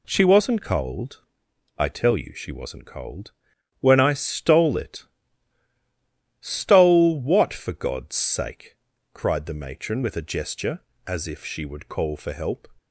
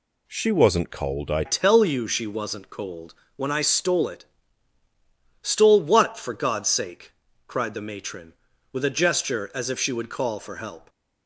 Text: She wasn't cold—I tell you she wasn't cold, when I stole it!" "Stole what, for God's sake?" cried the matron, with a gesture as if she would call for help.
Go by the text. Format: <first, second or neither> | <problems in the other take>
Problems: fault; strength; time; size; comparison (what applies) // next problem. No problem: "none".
first | changes voice at "tell"; from 1.4 s on; 9.4 s long